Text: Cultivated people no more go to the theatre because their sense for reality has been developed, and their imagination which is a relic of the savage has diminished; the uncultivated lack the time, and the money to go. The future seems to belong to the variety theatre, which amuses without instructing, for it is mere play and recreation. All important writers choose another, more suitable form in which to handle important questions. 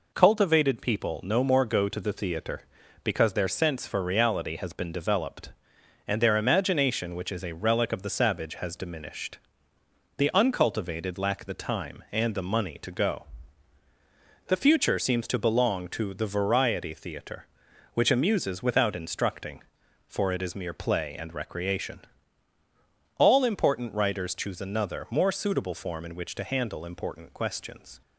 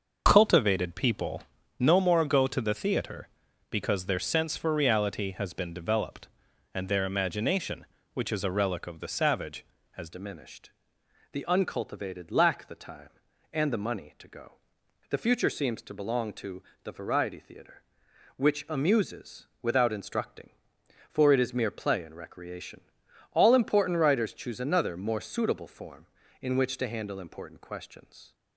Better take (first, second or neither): first